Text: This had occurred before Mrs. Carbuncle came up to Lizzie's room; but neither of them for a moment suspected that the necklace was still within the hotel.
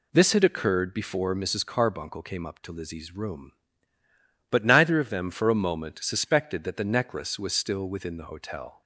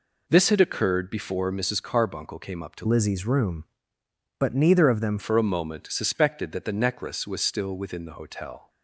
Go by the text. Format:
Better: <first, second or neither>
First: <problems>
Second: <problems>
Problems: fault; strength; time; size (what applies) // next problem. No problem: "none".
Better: first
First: none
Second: changes voice from "Lizzie's" to "them"; from 2.8 to 5.1 s; 2.3 s long